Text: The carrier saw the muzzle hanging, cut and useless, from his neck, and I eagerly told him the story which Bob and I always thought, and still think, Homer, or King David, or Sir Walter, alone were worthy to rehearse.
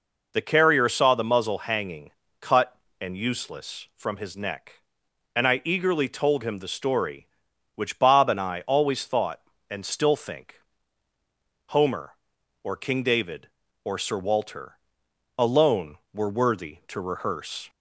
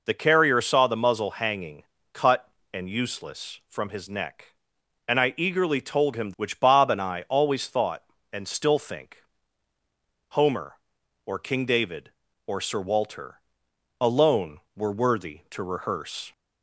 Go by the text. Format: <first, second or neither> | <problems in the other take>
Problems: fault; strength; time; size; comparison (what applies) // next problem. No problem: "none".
first | skips "the story"; at 6.3 s